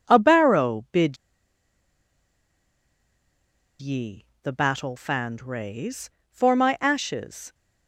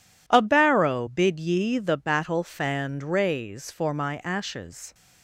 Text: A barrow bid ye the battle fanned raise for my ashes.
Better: second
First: pauses between "bid" and "ye"; strong; at 1.1 s; 2.6 s long // pauses between "ye" and "the"; slight; at 4.2 s; 0.16 s long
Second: none

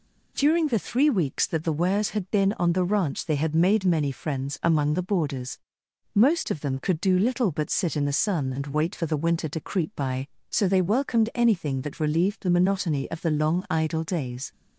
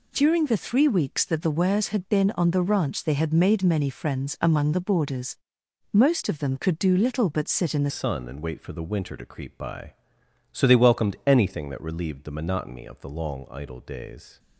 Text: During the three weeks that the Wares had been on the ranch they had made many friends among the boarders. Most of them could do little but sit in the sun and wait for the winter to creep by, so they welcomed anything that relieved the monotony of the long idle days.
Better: first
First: none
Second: changes voice at "sun"; from 7.8 s on; 6.5 s long

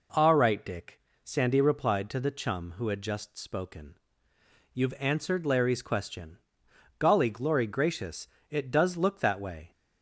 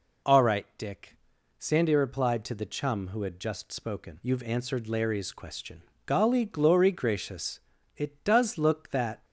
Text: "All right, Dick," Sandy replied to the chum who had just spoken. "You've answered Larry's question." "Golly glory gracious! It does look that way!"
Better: first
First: none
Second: stops before "way"; at 9.2 s

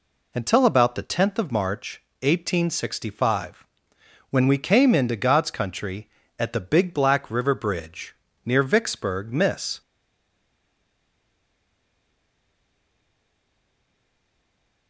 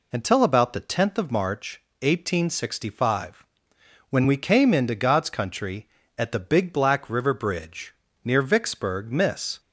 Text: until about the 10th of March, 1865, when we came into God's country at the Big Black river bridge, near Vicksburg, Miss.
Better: second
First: stays silent after the last word; strong; from 9.8 s on; 5.0 s long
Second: none

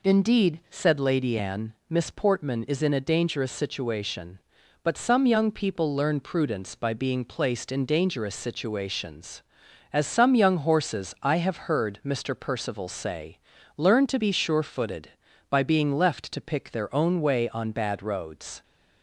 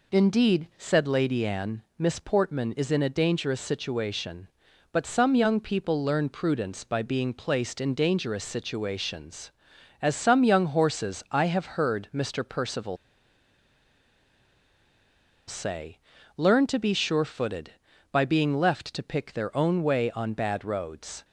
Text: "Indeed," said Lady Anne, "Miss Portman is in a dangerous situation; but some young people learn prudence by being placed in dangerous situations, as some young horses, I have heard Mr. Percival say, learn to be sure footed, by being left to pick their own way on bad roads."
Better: first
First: none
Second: pauses between "Percival" and "say"; strong; at 12.9 s; 2.5 s long

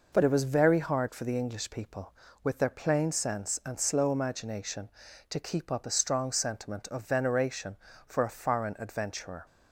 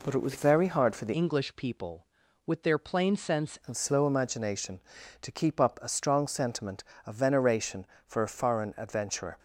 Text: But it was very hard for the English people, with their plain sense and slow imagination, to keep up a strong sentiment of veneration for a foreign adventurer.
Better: first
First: none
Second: changes voice from "English" to "sense"; from 1.1 to 3.5 s; 2.4 s long

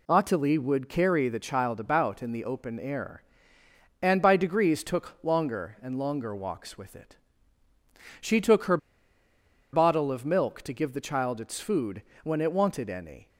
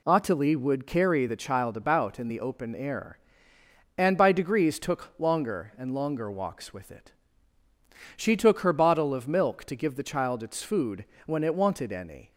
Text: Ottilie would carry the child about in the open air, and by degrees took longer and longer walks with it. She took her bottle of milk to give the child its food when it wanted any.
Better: second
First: pauses between "her" and "bottle"; noticeable; at 8.7 s; 0.95 s long // pauses between "food" and "when"; slight; at 12.0 s; 0.22 s long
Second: pauses between "food" and "when"; slight; at 11.0 s; 0.22 s long

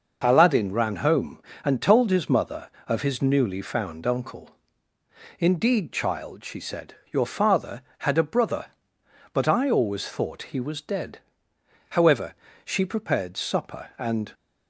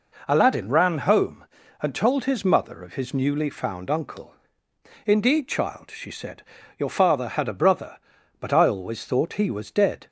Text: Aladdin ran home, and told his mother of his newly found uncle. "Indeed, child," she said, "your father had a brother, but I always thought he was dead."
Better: second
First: goes on to say "However she prepared supper and"; strong; from 11.9 s on; 2.4 s long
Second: none

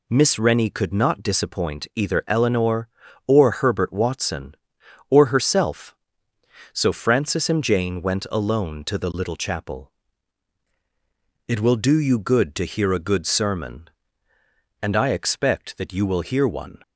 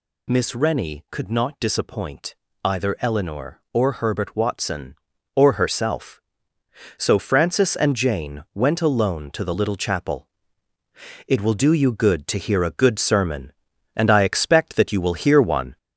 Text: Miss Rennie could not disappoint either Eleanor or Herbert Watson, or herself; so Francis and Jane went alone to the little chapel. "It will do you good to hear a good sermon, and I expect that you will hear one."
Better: first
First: none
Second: gets louder; slight; throughout; 3.5 dB // pauses between "disappoint" and "either"; slight; at 2.3 s; 0.28 s long

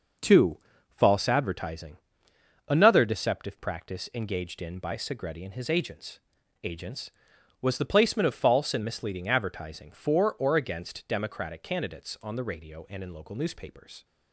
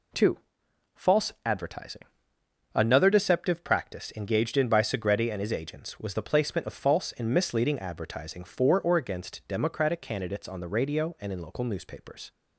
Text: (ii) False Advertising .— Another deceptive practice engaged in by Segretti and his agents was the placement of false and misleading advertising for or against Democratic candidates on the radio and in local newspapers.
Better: second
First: says "agents" twice; at 6.6 s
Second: none

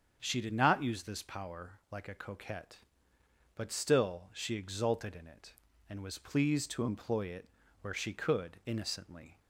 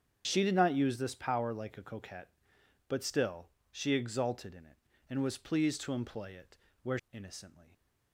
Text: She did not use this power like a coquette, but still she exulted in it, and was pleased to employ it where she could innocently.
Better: first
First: starts louder than the rest; strong; until 1.2 s; 7.5 dB // pauses between "it" and "where"; slight; at 7.4 s; 0.32 s long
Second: starts louder than the rest; strong; until 1.2 s; 8 dB // pauses between "still" and "she"; slight; at 3.4 s; 0.20 s long // pauses between "it" and "where"; slight; at 6.5 s; 0.24 s long // skips "she could"; at 7.0 s

